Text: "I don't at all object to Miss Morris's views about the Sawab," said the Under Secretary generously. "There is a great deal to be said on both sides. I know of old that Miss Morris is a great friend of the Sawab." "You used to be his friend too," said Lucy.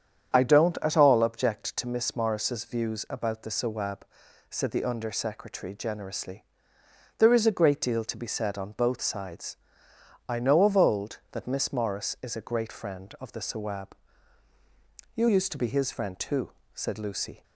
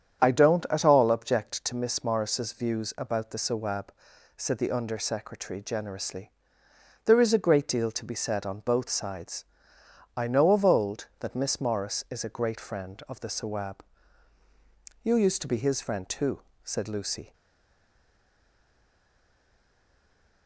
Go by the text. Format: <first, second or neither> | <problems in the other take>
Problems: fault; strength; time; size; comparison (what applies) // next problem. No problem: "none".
first | starts louder than the rest; strong; until 1.2 s; 8.5 dB; strong in the first // stays silent after the last word; strong; from 17.3 s on; 3.1 s long